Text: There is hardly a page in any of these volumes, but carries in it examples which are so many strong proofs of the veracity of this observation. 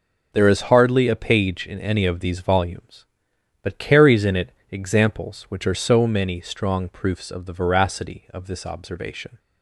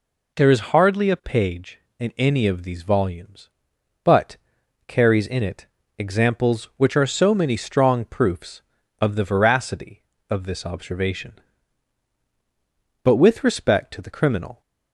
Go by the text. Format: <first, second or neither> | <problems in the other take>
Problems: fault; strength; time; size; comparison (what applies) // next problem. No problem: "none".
first | pauses between "but" and "carries"; noticeable; at 4.3 s; 0.50 s long // pauses between "it" and "examples"; slight; at 5.6 s; 0.30 s long; slight in the first // goes on to say "But with respect to the criminal"; from 13.0 s on; 1.5 s long